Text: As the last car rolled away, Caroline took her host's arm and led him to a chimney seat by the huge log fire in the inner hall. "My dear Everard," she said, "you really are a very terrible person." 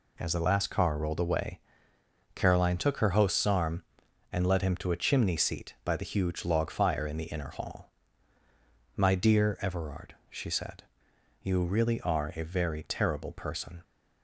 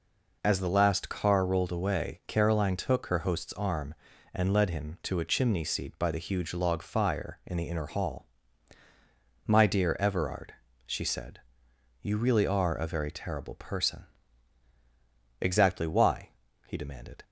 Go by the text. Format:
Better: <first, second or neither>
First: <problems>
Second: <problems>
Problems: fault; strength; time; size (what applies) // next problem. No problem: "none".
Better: first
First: none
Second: goes on to say "Exactly why he demanded"; strong; from 15.4 s on; 1.8 s long